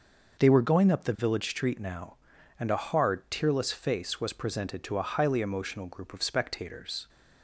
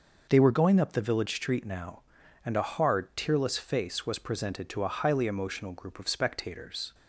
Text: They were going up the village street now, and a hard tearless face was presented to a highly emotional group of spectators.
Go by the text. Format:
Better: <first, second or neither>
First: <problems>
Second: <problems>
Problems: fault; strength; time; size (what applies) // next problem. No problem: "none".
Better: neither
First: none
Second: none